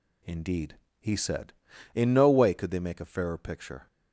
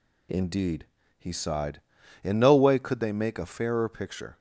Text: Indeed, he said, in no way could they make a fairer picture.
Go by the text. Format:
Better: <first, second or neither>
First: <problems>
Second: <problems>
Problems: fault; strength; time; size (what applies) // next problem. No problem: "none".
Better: first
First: none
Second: says "sighed" for "said"; at 1.3 s